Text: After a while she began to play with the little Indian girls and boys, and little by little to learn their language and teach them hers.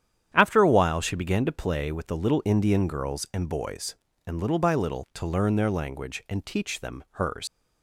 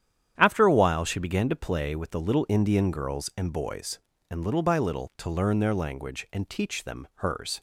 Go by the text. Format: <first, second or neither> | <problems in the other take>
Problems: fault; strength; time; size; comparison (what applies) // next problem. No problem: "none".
second | starts louder than the rest; strong; until 1.3 s; 9.5 dB; strong in the second // leaves "hers" unfinished; at 7.4 s; 95 ms